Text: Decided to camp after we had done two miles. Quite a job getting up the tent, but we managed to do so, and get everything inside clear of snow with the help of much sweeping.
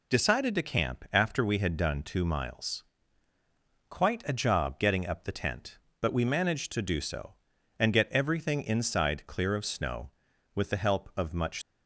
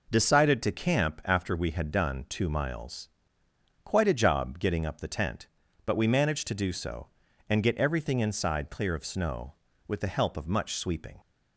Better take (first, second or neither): second